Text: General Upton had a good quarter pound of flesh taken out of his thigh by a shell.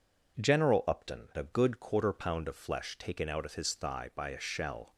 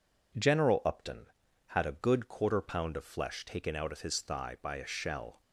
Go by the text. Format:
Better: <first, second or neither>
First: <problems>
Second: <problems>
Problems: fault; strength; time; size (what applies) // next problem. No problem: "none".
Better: second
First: skips "had"; at 1.3 s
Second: none